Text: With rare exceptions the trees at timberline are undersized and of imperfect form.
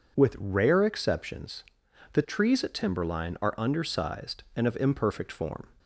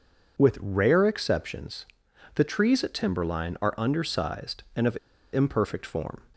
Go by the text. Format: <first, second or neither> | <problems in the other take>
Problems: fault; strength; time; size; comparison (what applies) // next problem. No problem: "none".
first | pauses between "exceptions" and "the"; noticeable; at 1.8 s; 0.52 s long; noticeable in the first // pauses between "of" and "imperfect"; at 4.9 s; 0.36 s long